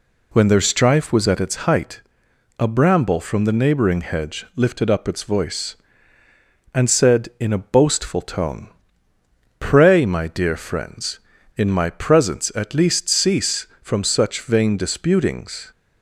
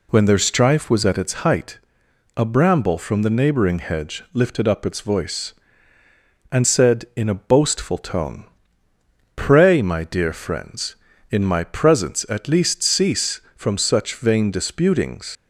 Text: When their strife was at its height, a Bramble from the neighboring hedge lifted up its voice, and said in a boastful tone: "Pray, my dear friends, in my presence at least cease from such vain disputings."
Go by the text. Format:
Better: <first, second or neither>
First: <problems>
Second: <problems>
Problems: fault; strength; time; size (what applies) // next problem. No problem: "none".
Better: first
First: none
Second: leaves "disputings" unfinished; at 15.3 s; 95 ms